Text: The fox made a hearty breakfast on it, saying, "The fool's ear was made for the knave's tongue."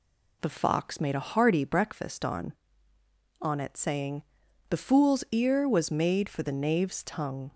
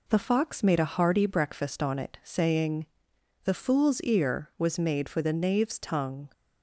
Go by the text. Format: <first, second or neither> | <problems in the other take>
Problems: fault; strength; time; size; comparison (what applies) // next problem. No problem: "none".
second | says "on" twice; at 3.4 s